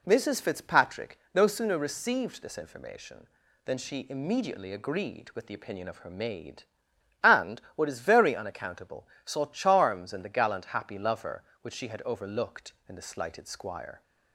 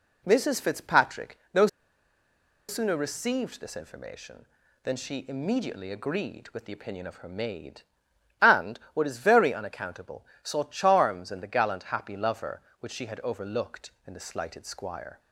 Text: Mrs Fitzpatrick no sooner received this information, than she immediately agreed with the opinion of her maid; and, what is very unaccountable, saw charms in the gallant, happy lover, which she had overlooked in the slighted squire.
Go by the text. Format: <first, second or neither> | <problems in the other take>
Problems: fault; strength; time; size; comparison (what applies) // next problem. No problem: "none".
first | pauses between "Fitzpatrick" and "no"; slight; at 1.3 s; 0.16 s long; slight in the first // pauses between "no" and "sooner"; at 1.6 s; 1.0 s long